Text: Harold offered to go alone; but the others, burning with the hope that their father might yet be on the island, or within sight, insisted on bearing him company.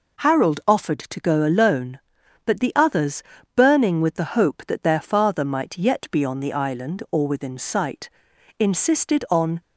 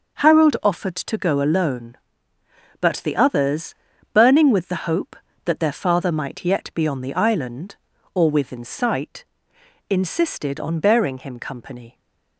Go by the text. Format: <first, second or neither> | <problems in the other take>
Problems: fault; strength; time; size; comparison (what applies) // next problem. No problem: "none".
second | stops before "bearing him company"; at 9.6 s